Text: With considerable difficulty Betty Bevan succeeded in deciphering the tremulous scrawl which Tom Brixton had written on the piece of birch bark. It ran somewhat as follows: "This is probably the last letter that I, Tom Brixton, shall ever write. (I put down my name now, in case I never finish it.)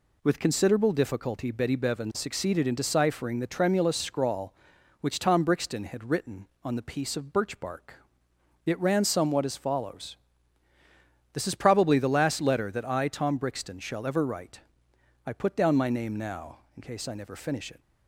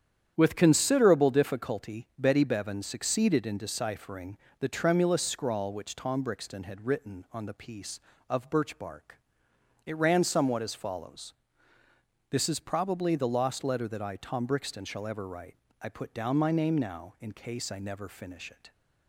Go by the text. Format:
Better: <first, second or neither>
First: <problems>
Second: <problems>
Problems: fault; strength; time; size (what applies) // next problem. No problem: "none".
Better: first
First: none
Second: starts louder than the rest; strong; until 1.3 s; 9 dB // pauses between "deciphering" and "the"; slight; at 4.3 s; 0.24 s long // says "lost" for "last"; at 13.2 s